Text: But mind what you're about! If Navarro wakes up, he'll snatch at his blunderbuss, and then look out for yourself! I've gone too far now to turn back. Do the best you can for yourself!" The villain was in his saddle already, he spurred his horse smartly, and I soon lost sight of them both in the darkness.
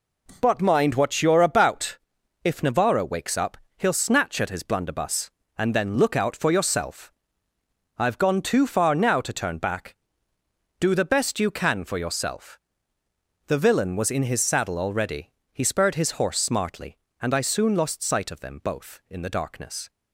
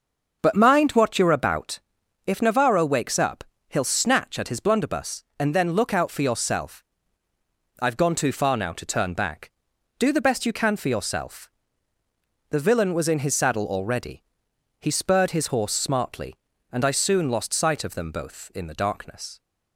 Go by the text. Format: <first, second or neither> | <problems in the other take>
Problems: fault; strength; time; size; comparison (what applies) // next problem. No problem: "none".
first | starts louder than the rest; until 1.8 s; 6.5 dB